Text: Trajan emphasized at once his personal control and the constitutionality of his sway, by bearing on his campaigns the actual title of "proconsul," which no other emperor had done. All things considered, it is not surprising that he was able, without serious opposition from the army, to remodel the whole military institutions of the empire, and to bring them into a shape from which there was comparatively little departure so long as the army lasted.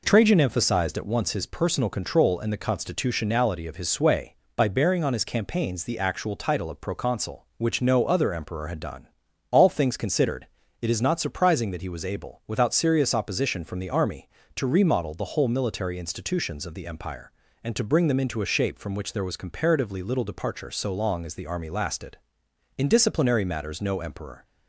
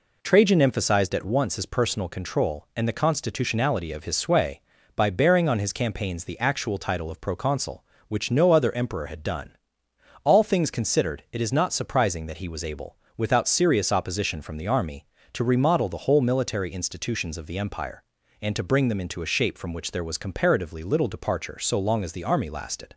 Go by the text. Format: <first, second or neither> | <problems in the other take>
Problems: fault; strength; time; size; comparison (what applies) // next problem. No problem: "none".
second | goes on to say "In disciplinary matters no emperor"; strong; from 22.7 s on; 1.6 s long